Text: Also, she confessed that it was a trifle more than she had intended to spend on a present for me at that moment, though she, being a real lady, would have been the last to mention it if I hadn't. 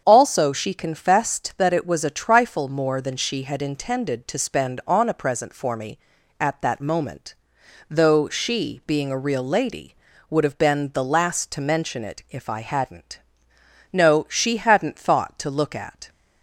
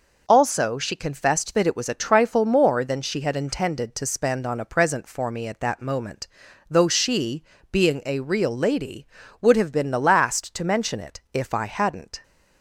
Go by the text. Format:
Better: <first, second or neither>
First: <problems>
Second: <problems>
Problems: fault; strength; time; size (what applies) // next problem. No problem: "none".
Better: second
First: starts louder than the rest; strong; until 1.0 s; 7.5 dB // goes on to say "No she hadn't thought to look at"; strong; from 13.9 s on; 2.1 s long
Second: none